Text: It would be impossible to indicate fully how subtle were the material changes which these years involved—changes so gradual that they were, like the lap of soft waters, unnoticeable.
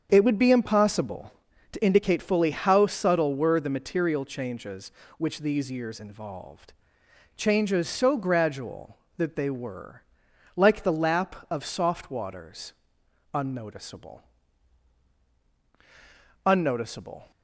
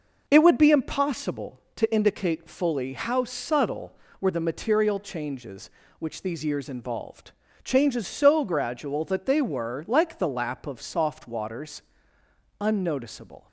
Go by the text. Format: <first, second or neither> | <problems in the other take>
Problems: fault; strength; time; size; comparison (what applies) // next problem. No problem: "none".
second | starts louder than the rest; until 1.1 s; 7 dB // says "unnoticeable" twice; at 16.4 s